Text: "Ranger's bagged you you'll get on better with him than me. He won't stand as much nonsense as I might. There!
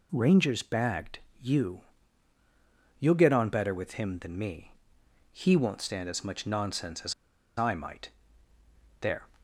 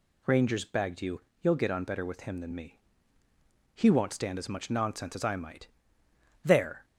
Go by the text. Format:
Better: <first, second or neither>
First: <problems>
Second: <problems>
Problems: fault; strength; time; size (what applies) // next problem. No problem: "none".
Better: second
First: pauses between "bagged" and "you"; slight; at 1.1 s; 0.22 s long // pauses between "you" and "you'll"; at 1.8 s; 1.1 s long // pauses between "as" and "I"; at 7.1 s; 0.44 s long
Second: pauses between "you" and "you'll"; slight; at 1.2 s; 0.20 s long